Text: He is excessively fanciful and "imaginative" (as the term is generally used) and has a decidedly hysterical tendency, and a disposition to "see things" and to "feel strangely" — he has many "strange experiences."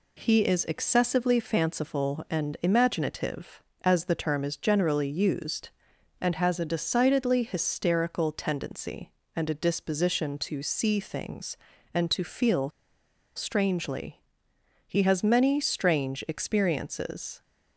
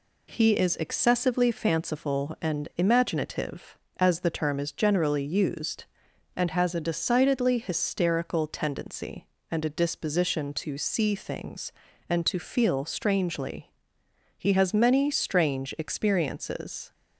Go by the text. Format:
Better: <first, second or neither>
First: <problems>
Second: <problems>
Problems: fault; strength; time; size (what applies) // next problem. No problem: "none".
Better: second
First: pauses between "feel" and "strangely"; noticeable; at 12.7 s; 0.65 s long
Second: none